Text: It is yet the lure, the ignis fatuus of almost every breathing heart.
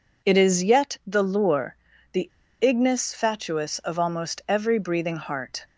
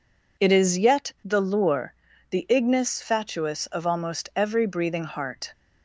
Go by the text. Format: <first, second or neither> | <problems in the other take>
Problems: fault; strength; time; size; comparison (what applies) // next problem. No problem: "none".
second | pauses between "the" and "ignis"; slight; at 2.2 s; 0.32 s long